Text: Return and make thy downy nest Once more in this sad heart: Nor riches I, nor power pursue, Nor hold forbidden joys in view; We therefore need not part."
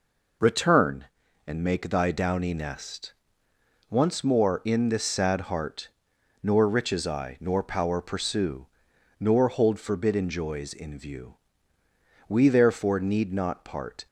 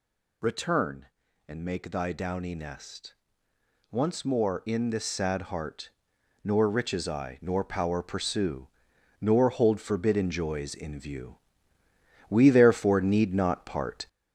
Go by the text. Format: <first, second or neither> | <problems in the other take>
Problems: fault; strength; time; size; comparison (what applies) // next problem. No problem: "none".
first | gets louder; noticeable; throughout; 4 dB // pauses between "nest" and "Once"; noticeable; at 3.1 s; 0.76 s long; noticeable in the first